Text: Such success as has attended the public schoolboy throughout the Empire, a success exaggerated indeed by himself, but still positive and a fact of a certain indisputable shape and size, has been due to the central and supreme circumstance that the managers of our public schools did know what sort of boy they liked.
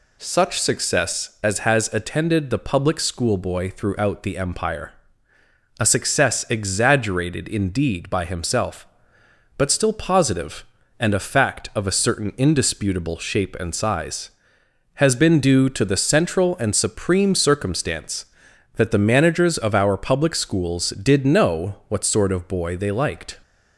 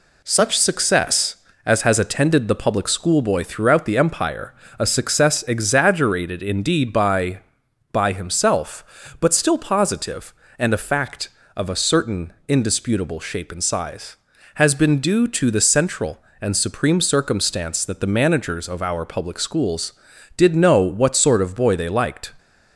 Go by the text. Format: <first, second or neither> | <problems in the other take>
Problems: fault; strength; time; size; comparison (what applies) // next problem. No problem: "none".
first | says "by" twice; at 7.9 s